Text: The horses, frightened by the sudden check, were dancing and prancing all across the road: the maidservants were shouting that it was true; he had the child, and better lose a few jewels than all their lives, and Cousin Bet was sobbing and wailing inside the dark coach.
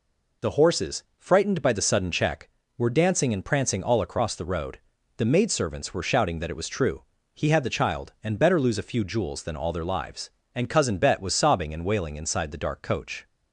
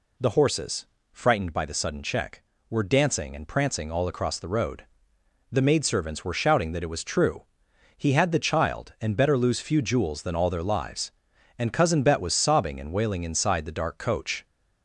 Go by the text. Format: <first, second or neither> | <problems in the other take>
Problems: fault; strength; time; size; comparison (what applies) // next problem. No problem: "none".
first | skips "a"; at 9.5 s